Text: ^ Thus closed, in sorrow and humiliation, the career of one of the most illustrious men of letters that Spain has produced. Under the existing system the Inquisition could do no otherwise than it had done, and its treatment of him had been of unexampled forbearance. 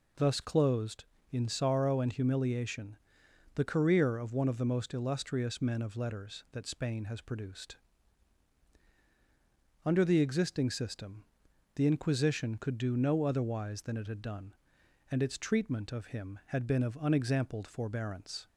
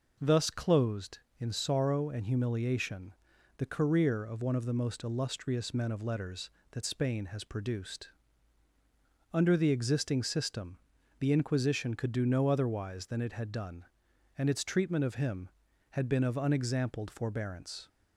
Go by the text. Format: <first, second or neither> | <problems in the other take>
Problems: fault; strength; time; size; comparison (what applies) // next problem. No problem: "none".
neither | pauses between "system" and "the"; the same in both